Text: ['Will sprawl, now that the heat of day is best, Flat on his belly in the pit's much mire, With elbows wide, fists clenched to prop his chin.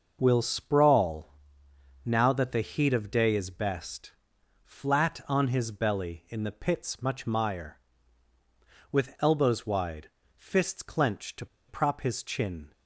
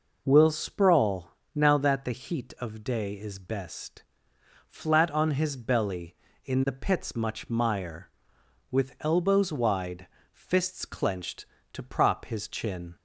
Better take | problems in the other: second | starts louder than the rest; noticeable; until 1.2 s; 6 dB // pauses between "to" and "prop"; slight; at 11.4 s; 0.22 s long

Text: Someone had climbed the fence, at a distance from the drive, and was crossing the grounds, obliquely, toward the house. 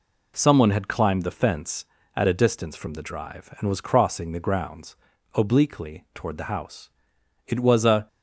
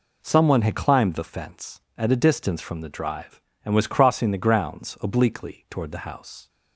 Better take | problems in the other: second | goes on to say "It was a"; noticeable; from 7.4 s on; 0.62 s long

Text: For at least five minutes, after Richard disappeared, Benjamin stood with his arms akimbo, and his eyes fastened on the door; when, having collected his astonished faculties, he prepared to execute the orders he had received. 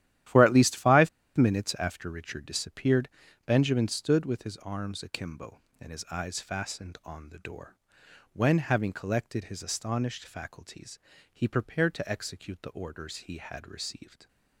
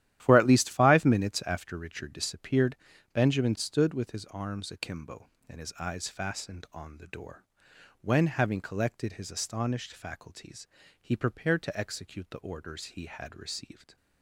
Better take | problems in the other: second | starts louder than the rest; strong; until 1.5 s; 12.5 dB; strong in the second // pauses between "five" and "minutes"; slight; at 1.0 s; 0.26 s long

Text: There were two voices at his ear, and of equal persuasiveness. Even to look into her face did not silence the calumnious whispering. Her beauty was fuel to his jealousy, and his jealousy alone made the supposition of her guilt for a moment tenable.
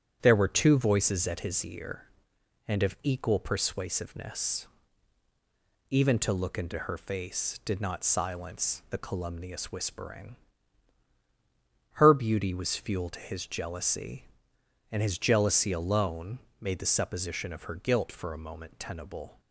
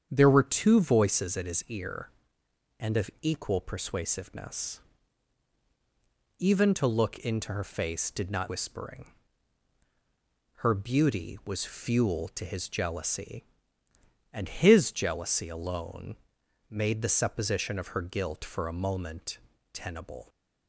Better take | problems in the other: first | starts louder than the rest; strong; until 1.1 s; 8 dB; strong in the first // skips "silence the calumnious"; at 8.4 s // pauses between "alone" and "made"; noticeable; at 16.1 s; 0.54 s long; slight in the first // pauses between "moment" and "tenable"; slight; at 19.3 s; 0.34 s long

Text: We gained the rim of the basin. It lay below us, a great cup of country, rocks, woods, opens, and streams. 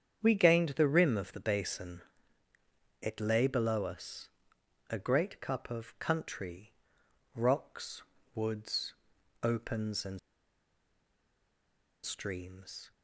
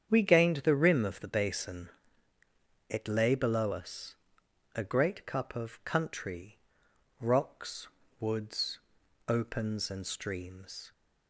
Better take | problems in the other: second | starts louder than the rest; strong; until 1.2 s; 8.5 dB; strong in the second // pauses between "and" and "streams"; strong; at 10.1 s; 1.8 s long

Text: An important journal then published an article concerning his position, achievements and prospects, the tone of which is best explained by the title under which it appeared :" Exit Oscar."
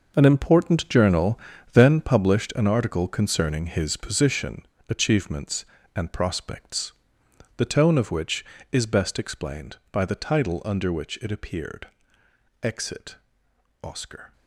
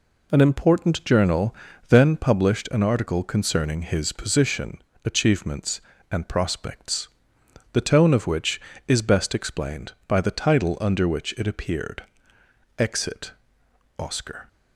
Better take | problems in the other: second | gets quieter; strong; throughout; 16 dB // pauses between "journal" and "then"; slight; at 1.3 s; 0.32 s long; slight in the second // pauses between "Exit" and "Oscar"; noticeable; at 13.1 s; 0.66 s long; noticeable in the second

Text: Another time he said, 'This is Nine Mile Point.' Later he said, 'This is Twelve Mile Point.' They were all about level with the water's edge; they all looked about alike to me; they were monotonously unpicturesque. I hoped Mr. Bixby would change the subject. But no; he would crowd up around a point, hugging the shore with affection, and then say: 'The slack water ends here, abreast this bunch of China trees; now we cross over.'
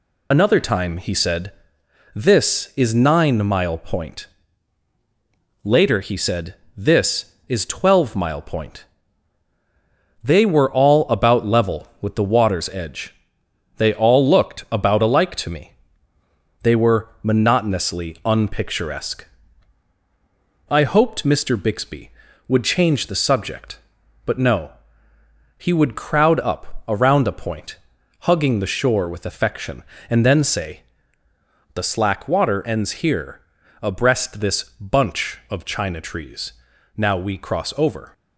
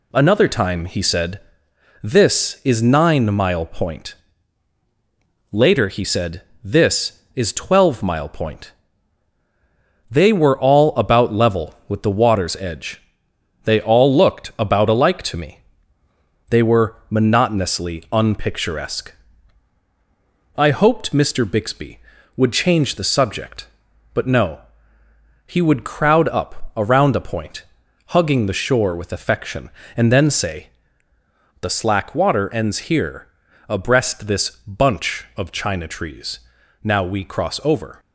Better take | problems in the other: second | loses the start of "Another"; at 0.3 s; 55 ms // pauses between "this" and "bunch"; slight; at 34.6 s; 0.16 s long; slight in the second

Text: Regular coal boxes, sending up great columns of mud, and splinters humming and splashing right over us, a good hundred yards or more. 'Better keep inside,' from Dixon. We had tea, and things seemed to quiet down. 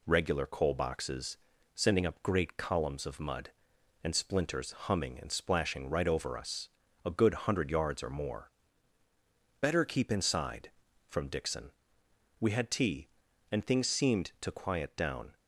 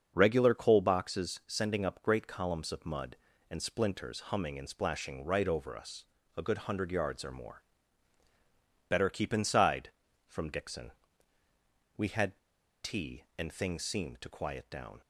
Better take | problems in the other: first | starts louder than the rest; until 1.1 s; 6.5 dB // pauses between "had" and "tea"; at 12.3 s; 0.44 s long

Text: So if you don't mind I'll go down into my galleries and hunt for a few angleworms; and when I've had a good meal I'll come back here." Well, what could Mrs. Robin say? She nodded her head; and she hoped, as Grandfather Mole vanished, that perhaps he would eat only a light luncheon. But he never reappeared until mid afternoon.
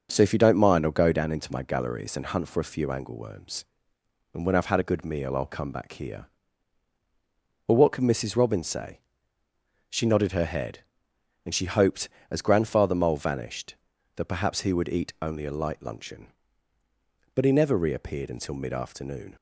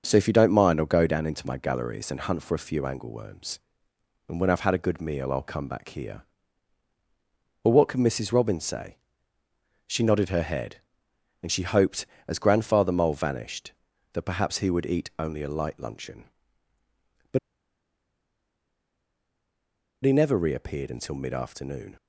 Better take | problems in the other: first | starts louder than the rest; until 1.0 s; 6.5 dB; also in the first // pauses between "But" and "he"; strong; at 17.3 s; 2.6 s long

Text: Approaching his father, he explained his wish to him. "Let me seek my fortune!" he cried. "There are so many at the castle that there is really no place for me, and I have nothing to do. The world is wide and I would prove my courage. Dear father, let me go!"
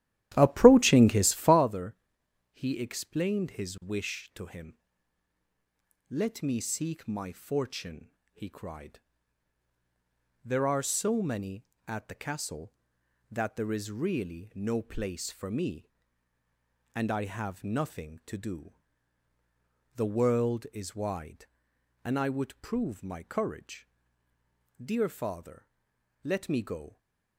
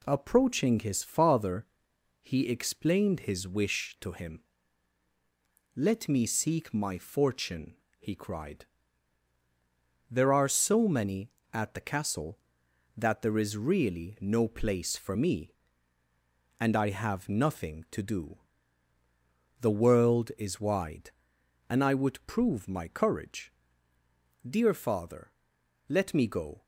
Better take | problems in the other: second | starts louder than the rest; strong; until 1.7 s; 13.5 dB

